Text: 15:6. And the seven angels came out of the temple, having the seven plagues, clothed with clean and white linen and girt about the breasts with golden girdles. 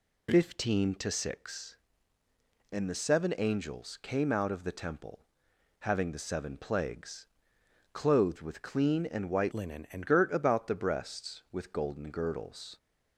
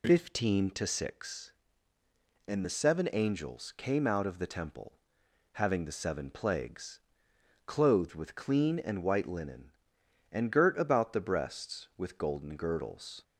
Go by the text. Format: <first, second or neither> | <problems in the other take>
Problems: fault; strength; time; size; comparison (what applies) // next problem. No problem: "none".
second | changes voice from "linen" to "and"; from 9.5 to 10.0 s; 0.5 s long